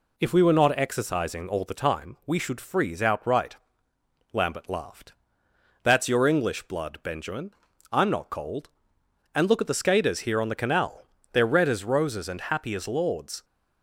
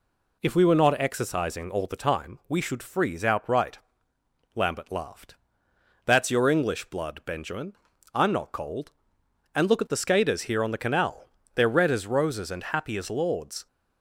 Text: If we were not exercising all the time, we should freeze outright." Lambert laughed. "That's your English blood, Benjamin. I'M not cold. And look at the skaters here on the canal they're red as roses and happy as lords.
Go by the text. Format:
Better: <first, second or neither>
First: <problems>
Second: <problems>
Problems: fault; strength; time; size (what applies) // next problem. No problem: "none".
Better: neither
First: pauses between "canal" and "they're"; slight; at 11.0 s; 0.28 s long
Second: pauses between "canal" and "they're"; slight; at 11.2 s; 0.28 s long